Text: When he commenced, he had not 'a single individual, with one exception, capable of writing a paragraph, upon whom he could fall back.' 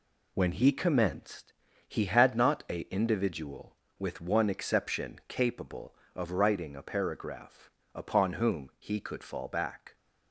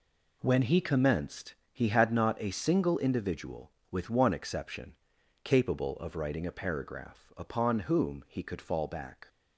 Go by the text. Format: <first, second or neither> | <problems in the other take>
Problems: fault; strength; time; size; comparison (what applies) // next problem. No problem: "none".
second | skips "single"; at 2.8 s